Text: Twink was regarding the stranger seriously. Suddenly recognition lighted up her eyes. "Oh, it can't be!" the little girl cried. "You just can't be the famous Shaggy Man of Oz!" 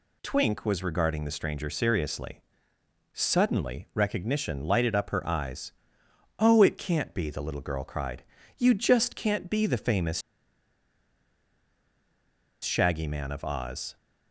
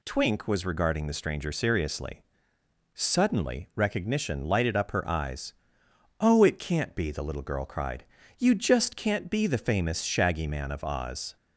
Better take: second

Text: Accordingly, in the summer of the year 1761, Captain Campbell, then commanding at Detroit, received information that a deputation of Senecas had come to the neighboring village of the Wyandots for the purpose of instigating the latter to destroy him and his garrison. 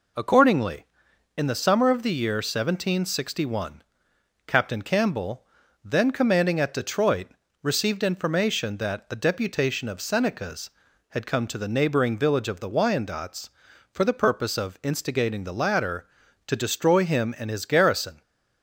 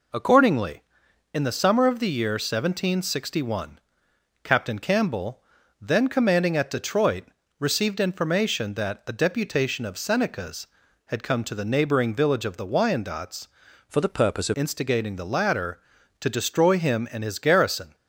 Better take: first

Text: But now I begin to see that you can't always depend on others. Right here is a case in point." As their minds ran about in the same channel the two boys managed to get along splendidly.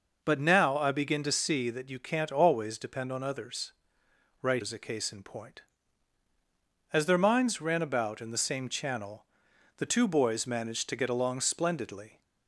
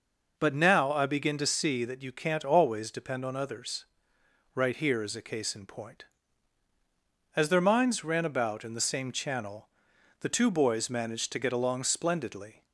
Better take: second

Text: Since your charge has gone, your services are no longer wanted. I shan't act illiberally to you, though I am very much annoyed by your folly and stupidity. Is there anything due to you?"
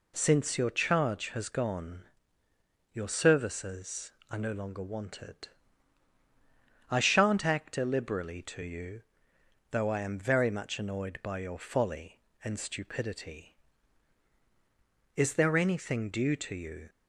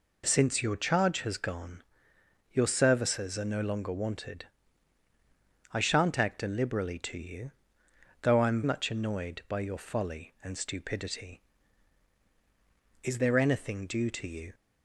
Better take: first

